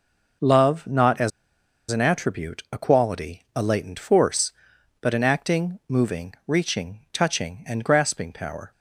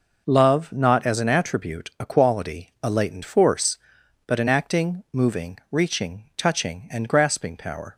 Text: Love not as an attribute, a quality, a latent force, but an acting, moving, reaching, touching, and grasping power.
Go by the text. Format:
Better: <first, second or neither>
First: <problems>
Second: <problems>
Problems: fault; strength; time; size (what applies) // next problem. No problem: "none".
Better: second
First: pauses between "as" and "an"; noticeable; at 1.3 s; 0.60 s long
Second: none